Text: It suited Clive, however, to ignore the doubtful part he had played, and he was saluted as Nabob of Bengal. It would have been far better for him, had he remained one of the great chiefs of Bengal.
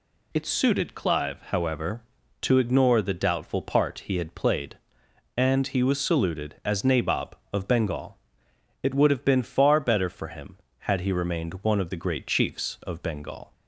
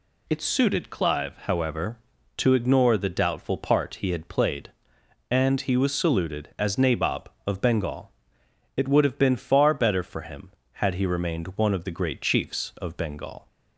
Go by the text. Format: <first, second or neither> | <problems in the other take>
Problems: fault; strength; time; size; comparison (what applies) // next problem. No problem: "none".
neither | none